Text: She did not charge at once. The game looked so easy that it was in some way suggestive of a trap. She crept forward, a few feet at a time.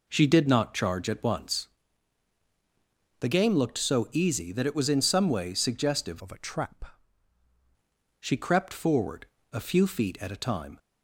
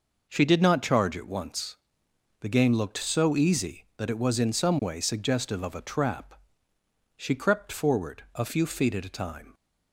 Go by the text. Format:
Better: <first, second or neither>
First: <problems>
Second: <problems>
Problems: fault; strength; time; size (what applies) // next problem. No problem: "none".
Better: second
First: changes voice from "of" to "trap"; from 6.1 to 6.9 s; 0.8 s long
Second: none